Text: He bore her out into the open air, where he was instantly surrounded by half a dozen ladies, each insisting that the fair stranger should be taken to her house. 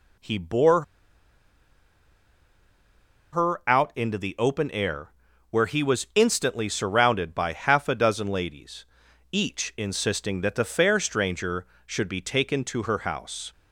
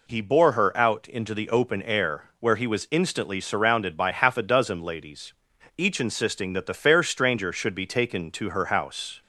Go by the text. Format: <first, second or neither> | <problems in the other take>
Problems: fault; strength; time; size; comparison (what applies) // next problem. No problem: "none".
second | pauses between "bore" and "her"; strong; at 0.8 s; 2.5 s long